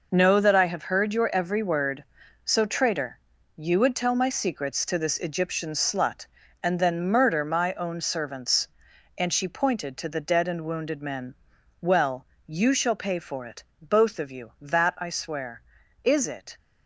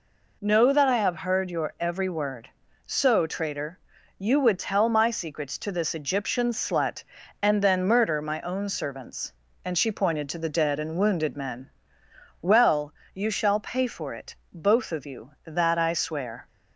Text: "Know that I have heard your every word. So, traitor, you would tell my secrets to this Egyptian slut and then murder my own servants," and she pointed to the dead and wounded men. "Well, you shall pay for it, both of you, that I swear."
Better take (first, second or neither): second